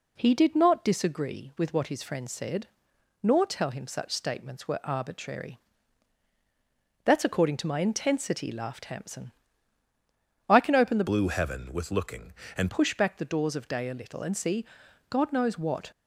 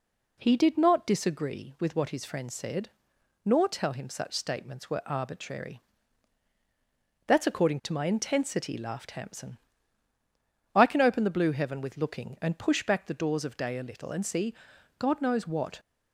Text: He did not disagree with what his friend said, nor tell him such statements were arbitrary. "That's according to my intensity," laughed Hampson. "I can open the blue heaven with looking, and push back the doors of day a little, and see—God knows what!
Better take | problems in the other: second | changes voice from "blue" to "and"; from 11.0 to 12.7 s; 1.7 s long

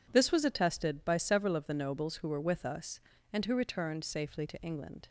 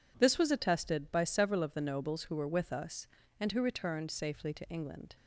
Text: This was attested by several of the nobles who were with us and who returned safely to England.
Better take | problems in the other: neither | none

